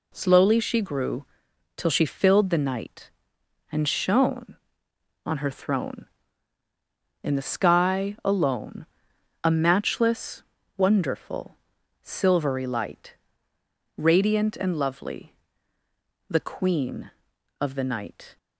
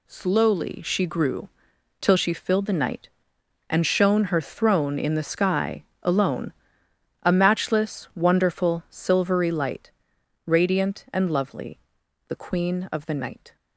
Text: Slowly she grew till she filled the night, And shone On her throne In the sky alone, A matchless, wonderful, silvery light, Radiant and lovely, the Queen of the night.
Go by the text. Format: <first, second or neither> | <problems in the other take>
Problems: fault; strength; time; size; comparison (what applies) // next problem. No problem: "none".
first | pauses between "grew" and "till"; noticeable; at 1.4 s; 0.50 s long; noticeable in the first // skips "On"; at 4.2 s // pauses between "sky" and "alone"; slight; at 5.8 s; 0.18 s long